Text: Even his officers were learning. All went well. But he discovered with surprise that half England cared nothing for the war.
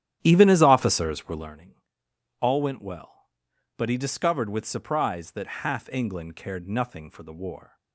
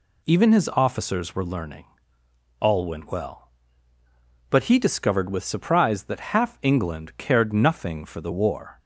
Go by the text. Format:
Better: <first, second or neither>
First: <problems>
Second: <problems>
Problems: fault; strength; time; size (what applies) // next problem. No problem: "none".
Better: second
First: starts louder than the rest; strong; until 1.6 s; 11.5 dB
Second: none